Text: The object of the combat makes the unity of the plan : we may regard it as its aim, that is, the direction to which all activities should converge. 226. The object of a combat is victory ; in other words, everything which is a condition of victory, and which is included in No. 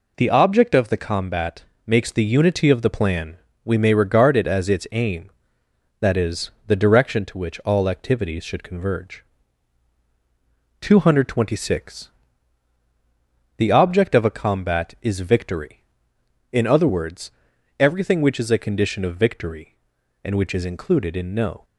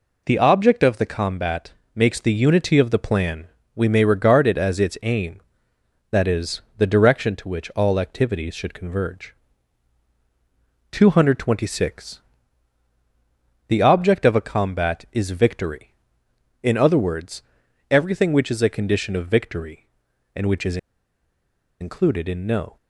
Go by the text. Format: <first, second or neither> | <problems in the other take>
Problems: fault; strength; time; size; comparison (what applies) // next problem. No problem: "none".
first | pauses between "combat" and "makes"; slight; at 1.7 s; 0.20 s long; slight in the first // pauses between "is" and "included"; at 20.7 s; 1.0 s long